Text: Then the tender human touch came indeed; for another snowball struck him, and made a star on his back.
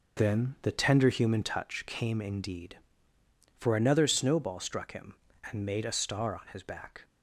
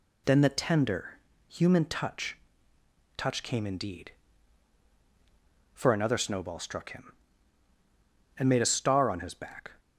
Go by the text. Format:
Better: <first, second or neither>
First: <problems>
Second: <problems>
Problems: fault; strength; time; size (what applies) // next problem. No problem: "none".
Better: first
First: none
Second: pauses between "tender" and "human"; slight; at 1.1 s; 0.28 s long // says "touch" twice; at 3.1 s